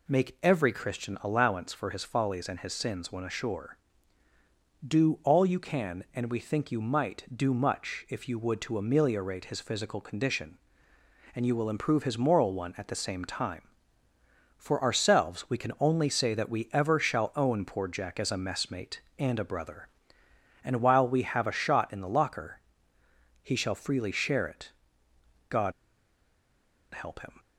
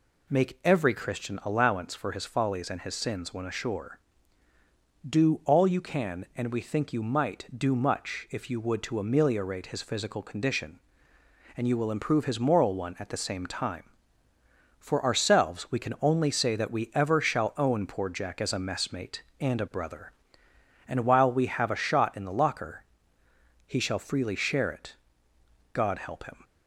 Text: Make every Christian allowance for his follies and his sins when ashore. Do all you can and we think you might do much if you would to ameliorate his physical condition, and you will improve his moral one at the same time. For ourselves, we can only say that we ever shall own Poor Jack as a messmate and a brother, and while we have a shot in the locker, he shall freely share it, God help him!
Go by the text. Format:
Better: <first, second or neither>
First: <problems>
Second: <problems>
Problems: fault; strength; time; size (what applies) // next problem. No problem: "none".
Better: second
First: pauses between "God" and "help"; at 25.7 s; 1.2 s long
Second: none